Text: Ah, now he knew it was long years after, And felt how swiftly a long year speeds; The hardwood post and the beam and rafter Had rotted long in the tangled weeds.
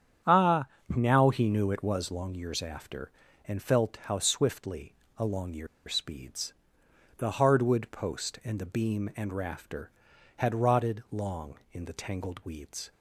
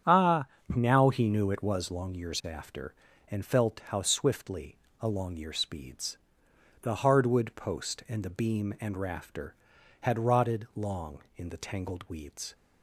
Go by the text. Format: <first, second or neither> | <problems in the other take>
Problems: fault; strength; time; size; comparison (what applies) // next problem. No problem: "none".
second | starts louder than the rest; strong; until 1.4 s; 8.5 dB; strong in the second // pauses between "swiftly" and "a"; slight; at 4.9 s; 0.22 s long; slight in the second // pauses between "year" and "speeds"; slight; at 5.6 s; 0.21 s long